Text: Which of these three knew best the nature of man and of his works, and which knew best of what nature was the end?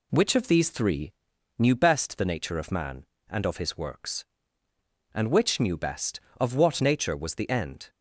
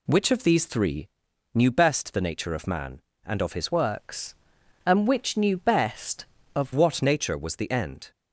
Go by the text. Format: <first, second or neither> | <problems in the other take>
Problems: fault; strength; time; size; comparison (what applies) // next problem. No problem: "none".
first | pauses between "three" and "knew"; at 1.0 s; 0.44 s long; also in the first // changes voice from "works" to "of"; from 3.7 to 6.7 s; 3.0 s long